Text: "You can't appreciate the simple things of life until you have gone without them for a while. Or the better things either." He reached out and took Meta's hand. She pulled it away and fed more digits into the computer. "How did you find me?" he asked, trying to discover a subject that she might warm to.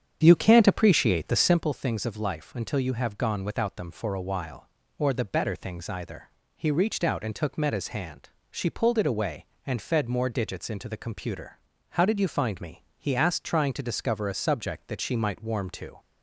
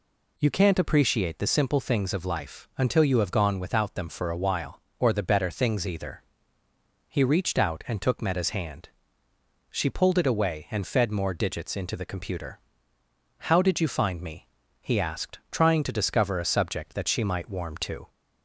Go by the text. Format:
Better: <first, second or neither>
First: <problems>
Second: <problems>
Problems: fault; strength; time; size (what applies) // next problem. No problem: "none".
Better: second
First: starts louder than the rest; strong; until 1.7 s; 8 dB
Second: none